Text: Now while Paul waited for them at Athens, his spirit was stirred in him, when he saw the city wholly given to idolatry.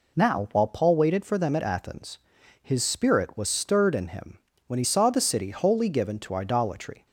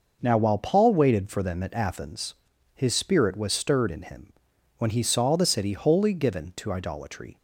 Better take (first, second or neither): neither